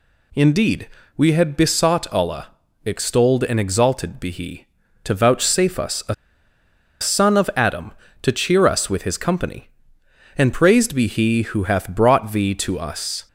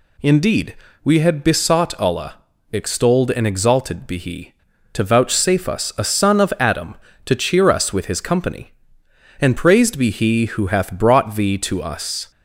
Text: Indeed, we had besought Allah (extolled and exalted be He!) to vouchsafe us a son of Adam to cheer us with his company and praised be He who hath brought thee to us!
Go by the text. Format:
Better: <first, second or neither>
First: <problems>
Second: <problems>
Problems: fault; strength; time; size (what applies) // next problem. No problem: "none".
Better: second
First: pauses between "a" and "son"; noticeable; at 6.1 s; 0.87 s long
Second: none